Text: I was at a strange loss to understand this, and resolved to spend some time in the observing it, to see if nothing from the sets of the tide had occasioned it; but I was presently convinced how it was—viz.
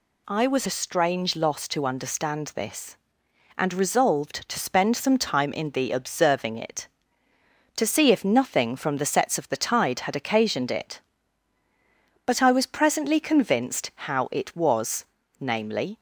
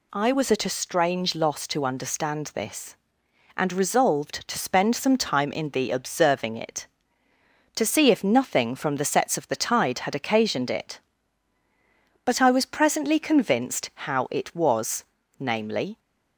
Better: second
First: skips "at"; at 0.6 s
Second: none

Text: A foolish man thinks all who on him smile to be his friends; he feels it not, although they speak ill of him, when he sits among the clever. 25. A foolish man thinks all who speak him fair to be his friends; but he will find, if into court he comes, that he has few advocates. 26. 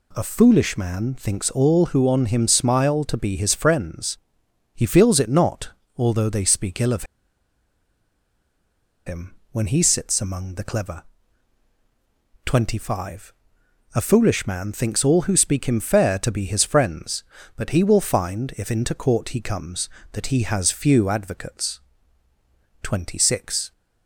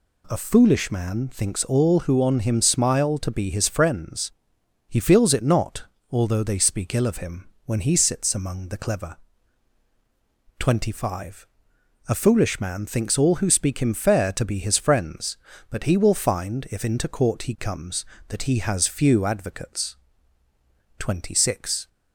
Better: second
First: pauses between "of" and "him"; strong; at 7.0 s; 2.0 s long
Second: none

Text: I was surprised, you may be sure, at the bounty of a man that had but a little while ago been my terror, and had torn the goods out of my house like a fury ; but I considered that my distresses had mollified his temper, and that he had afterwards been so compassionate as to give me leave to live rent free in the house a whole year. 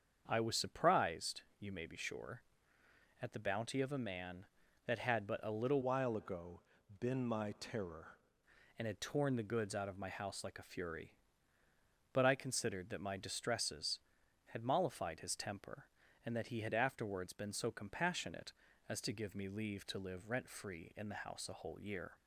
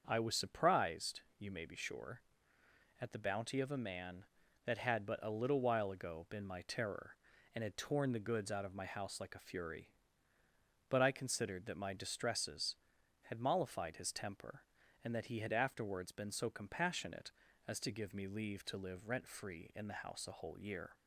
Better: second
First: starts louder than the rest; until 1.2 s; 7 dB // changes voice from "while" to "terror"; from 5.8 to 8.1 s; 2.3 s long // pauses between "ago" and "been"; at 6.6 s; 0.38 s long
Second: starts louder than the rest; until 1.0 s; 6.5 dB

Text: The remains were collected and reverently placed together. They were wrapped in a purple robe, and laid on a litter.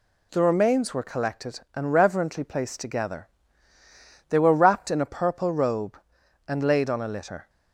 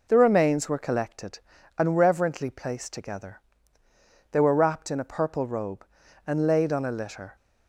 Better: neither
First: none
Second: none

